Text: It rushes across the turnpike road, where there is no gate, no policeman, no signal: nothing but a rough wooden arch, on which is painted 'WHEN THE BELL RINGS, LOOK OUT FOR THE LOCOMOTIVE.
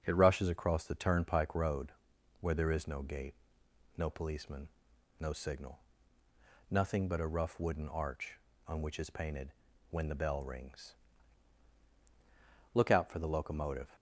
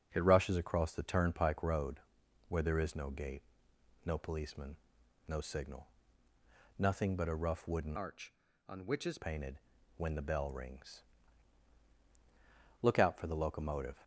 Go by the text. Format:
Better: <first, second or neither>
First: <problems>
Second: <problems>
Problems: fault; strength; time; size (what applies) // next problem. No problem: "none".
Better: first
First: starts louder than the rest; until 1.0 s; 6.5 dB // pauses between "painted" and "WHEN"; at 9.5 s; 0.38 s long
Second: starts louder than the rest; until 1.1 s; 6.5 dB // changes voice from "arch" to "is"; from 7.9 to 9.1 s; 1.2 s long // pauses between "painted" and "WHEN"; at 9.5 s; 0.38 s long